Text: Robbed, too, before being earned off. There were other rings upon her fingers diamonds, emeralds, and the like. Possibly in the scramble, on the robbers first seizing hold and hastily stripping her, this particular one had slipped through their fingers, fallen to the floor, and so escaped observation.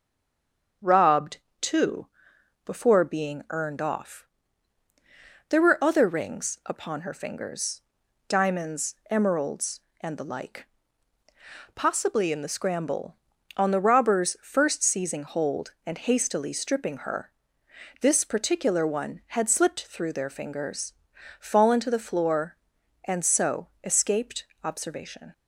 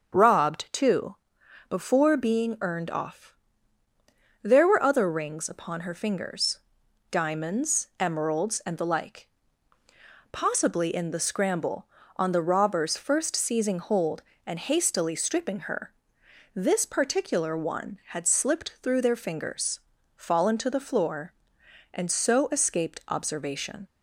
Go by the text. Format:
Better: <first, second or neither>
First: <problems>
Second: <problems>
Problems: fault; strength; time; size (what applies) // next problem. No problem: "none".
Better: second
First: stays silent before the first word; slight; until 0.8 s; 0.8 s long // starts louder than the rest; until 2.0 s; 7 dB // pauses between "fingers" and "diamonds"; noticeable; at 7.8 s; 0.48 s long // pauses between "escaped" and "observation"; slight; at 24.4 s; 0.18 s long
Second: starts louder than the rest; until 1.7 s; 7 dB // pauses between "fingers" and "diamonds"; noticeable; at 6.5 s; 0.50 s long